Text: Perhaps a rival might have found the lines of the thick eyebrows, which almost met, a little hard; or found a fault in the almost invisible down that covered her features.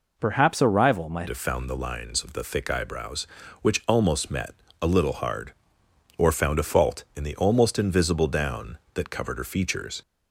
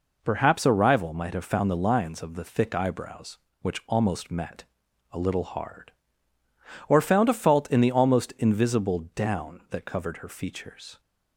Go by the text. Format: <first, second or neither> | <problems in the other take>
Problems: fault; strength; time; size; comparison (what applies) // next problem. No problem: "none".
second | changes voice at "have"; from 1.2 s on; 8.8 s long